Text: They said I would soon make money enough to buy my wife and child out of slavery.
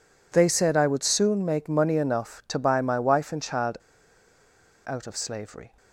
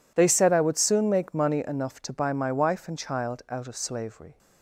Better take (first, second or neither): second